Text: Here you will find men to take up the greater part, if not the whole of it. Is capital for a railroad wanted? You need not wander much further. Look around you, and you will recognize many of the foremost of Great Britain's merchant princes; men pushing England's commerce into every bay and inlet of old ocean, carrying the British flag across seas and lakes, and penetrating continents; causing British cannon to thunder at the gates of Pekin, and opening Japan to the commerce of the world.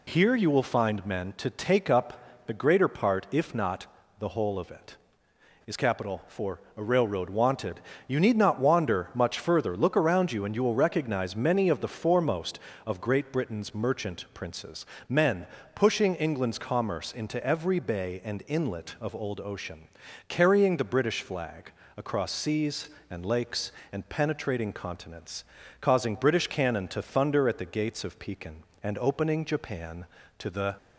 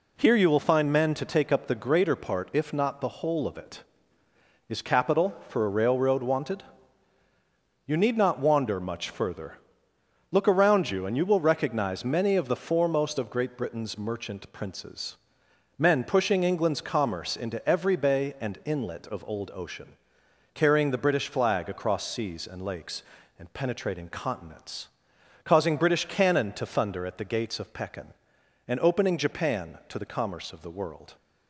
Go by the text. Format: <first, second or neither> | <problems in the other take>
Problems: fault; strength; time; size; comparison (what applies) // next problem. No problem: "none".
second | pauses between "not" and "the"; slight; at 3.8 s; 0.34 s long // pauses between "for" and "a"; slight; at 6.5 s; 0.18 s long // pauses between "men" and "pushing"; slight; at 15.4 s; 0.28 s long // pauses between "flag" and "across"; slight; at 21.7 s; 0.26 s long // stops before "commerce of the world"; at 30.7 s